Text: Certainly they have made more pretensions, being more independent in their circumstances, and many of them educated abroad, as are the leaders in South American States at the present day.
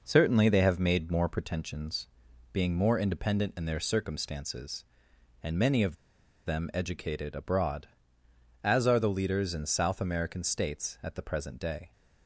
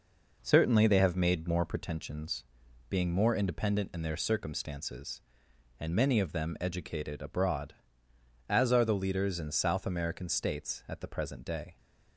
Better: second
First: pauses between "of" and "them"; noticeable; at 5.9 s; 0.50 s long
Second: none

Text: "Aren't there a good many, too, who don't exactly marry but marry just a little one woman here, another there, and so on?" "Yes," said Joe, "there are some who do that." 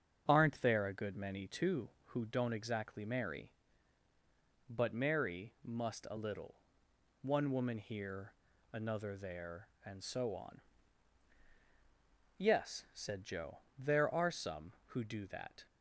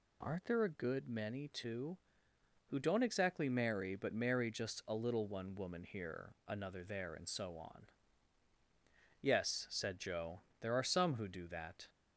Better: second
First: starts louder than the rest; strong; until 1.2 s; 7 dB // says "must" for "just"; at 5.6 s // pauses between "little" and "one"; noticeable; at 6.5 s; 0.66 s long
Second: none

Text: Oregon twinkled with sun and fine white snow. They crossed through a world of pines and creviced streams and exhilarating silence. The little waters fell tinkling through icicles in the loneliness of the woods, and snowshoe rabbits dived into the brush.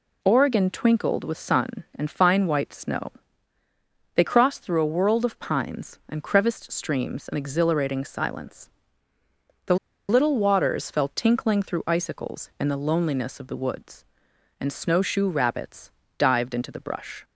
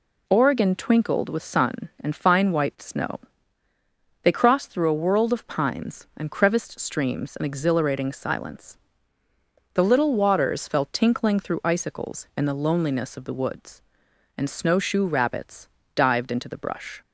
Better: second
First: pauses between "The" and "little"; slight; at 9.7 s; 0.33 s long // pauses between "rabbits" and "dived"; slight; at 15.8 s; 0.28 s long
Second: pauses between "rabbits" and "dived"; slight; at 15.6 s; 0.28 s long

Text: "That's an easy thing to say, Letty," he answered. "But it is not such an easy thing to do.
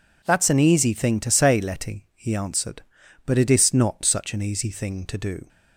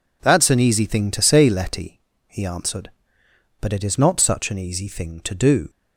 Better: neither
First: none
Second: none

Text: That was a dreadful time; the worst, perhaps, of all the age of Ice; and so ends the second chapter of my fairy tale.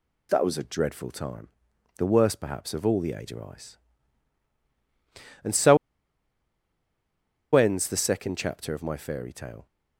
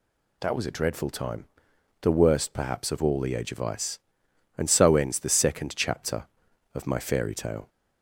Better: second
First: pauses between "so" and "ends"; strong; at 5.7 s; 1.7 s long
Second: none

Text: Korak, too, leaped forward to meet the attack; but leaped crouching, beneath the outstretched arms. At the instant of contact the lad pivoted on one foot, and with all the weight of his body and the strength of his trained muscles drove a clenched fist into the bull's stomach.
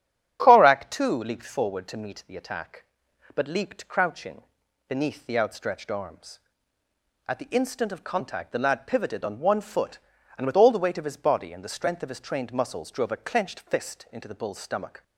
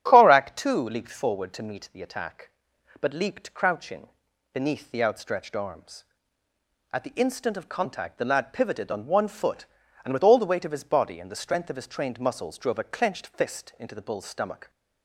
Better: neither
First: starts louder than the rest; strong; until 1.4 s; 9 dB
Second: starts louder than the rest; strong; until 1.0 s; 9 dB

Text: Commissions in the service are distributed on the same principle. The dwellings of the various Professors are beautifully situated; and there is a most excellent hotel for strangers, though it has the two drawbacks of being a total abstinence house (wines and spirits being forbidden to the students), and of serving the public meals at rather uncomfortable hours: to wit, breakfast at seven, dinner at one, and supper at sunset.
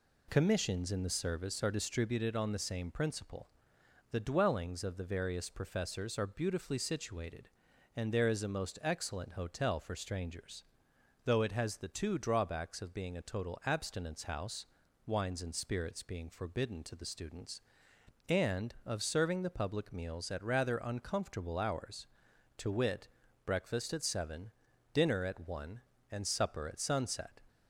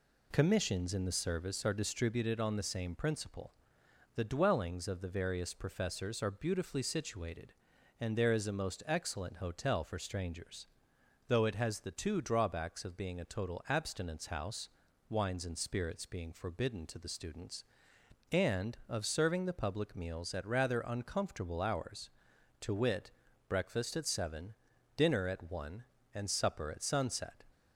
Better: neither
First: none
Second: none

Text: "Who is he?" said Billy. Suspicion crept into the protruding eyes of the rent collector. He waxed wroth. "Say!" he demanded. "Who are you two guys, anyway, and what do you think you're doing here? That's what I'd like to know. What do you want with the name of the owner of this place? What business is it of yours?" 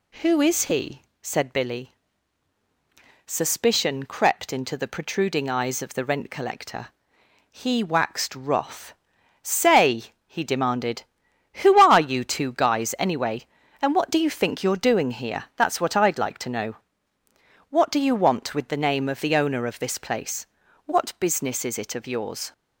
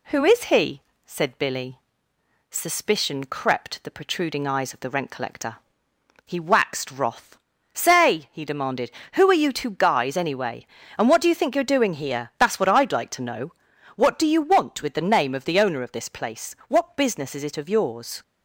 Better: first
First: none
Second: skips "into"; at 3.8 s

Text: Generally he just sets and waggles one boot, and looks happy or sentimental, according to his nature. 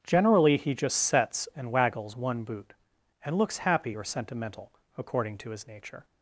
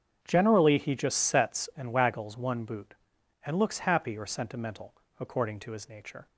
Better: neither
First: starts louder than the rest; strong; until 1.0 s; 7.5 dB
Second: starts louder than the rest; strong; until 1.2 s; 7.5 dB

